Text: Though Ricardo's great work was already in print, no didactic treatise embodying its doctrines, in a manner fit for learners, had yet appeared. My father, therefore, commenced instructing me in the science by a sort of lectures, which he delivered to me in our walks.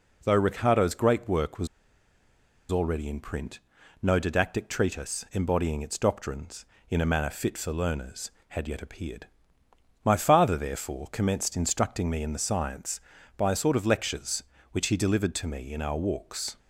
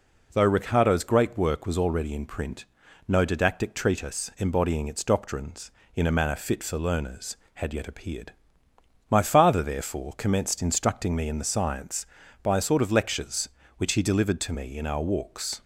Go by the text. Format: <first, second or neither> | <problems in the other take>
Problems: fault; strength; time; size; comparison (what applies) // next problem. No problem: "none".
second | pauses between "was" and "already"; at 1.6 s; 1.0 s long